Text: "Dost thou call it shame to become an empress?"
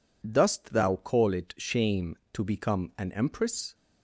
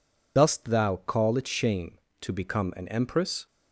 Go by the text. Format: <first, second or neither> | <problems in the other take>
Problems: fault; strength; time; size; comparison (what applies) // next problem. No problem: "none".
first | loses the start of "Dost"; at 0.3 s; 115 ms